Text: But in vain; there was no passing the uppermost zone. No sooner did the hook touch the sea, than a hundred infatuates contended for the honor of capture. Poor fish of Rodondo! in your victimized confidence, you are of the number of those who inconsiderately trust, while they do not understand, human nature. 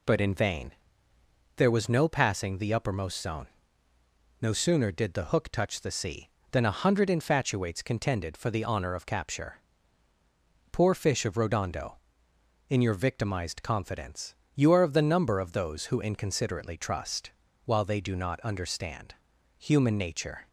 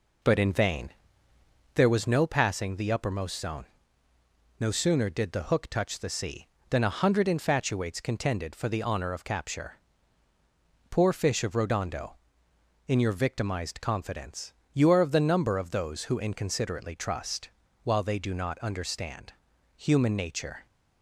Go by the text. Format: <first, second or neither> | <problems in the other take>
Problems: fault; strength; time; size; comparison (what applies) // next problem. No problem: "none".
first | starts louder than the rest; noticeable; until 2.1 s; 4 dB